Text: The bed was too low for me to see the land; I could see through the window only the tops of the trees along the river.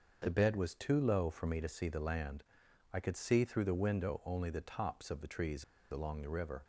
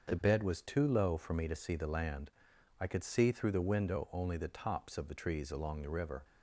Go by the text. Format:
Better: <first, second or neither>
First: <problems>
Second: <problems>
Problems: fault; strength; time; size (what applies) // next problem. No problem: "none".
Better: second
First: starts louder than the rest; until 1.2 s; 6.5 dB // pauses between "trees" and "along"; slight; at 5.6 s; 0.27 s long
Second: starts louder than the rest; until 1.1 s; 6.5 dB